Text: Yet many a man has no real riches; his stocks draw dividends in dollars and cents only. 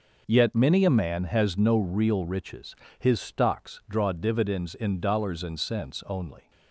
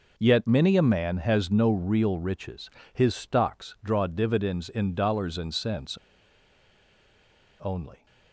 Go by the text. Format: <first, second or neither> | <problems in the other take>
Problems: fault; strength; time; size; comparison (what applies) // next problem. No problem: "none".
first | pauses between "cents" and "only"; strong; at 5.9 s; 1.6 s long